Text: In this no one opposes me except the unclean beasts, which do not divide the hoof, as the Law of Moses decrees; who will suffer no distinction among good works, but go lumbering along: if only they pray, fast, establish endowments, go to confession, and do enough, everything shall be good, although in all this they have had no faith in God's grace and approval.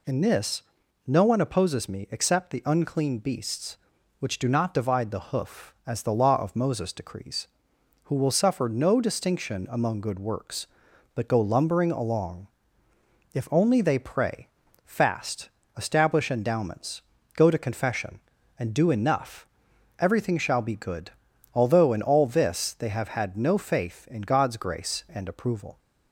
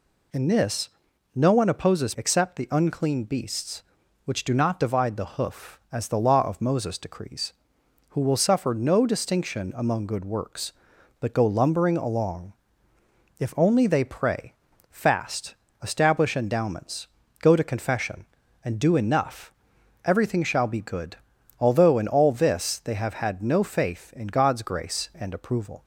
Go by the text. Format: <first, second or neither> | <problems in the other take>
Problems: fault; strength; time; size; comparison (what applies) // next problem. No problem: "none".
first | pauses between "this" and "no"; noticeable; at 0.8 s; 0.46 s long; also in the first // skips "me"; at 2.1 s